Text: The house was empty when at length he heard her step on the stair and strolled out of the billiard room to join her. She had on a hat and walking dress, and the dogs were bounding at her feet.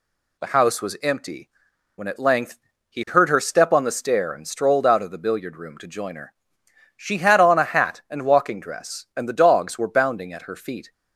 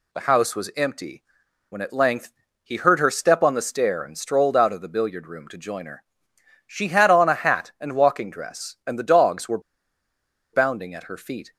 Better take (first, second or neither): first